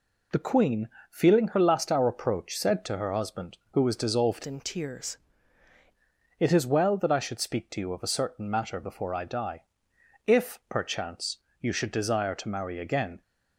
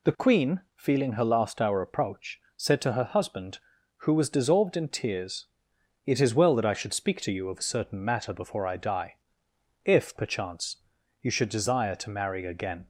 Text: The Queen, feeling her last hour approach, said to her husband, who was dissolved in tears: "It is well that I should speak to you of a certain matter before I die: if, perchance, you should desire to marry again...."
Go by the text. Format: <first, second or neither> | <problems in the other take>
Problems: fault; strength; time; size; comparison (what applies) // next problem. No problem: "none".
second | changes voice from "in" to "tears"; from 4.4 to 5.1 s; 0.7 s long